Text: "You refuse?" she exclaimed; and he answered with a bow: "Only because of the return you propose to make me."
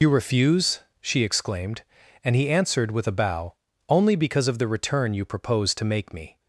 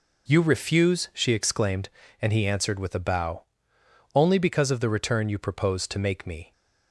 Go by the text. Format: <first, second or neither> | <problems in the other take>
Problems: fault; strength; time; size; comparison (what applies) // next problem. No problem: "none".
second | loses the start of "You"; at 0.0 s; 55 ms